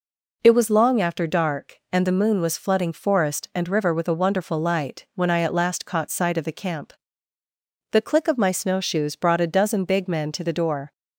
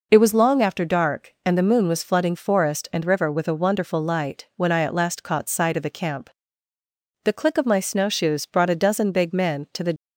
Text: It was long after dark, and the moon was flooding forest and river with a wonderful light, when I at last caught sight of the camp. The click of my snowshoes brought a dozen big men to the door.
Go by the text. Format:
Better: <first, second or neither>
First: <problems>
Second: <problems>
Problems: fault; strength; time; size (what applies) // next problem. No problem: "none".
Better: first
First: none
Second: stops before "door"; at 9.9 s